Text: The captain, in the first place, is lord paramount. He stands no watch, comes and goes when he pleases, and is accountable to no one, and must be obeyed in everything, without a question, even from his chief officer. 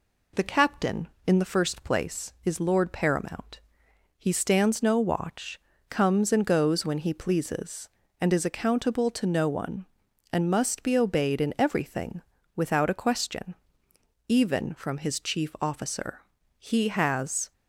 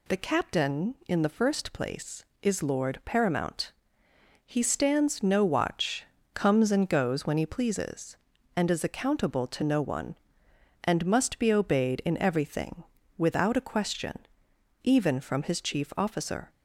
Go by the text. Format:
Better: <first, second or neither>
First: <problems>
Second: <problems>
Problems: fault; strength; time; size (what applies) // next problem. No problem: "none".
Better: second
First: goes on to say "He has"; noticeable; from 16.5 s on; 0.94 s long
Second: none